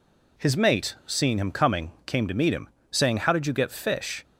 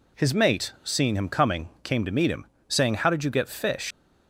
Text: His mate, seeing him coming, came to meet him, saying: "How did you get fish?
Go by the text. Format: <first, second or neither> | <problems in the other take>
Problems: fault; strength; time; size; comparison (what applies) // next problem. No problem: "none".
first | leaves "fish" unfinished; at 3.9 s; 100 ms